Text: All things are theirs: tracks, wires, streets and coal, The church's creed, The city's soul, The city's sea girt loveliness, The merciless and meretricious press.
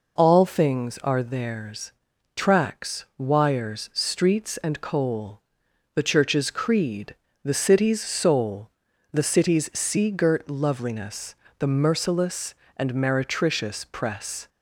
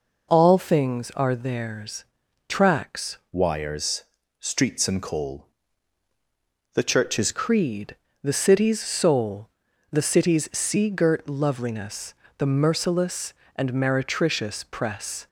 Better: first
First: none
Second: changes voice from "wires" to "church's"; from 3.3 to 7.3 s; 4.0 s long

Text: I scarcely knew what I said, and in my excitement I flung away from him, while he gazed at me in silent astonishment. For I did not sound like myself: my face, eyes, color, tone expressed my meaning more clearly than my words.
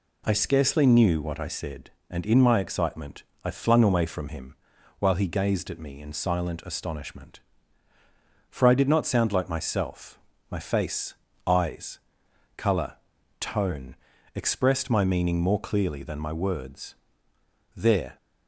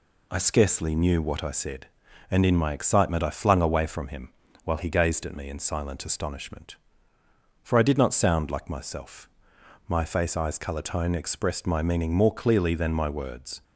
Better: second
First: pauses between "excitement" and "I"; slight; at 3.2 s; 0.20 s long // pauses between "tone" and "expressed"; at 13.9 s; 0.38 s long // goes on to say "There"; slight; from 17.7 s on; 0.40 s long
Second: none

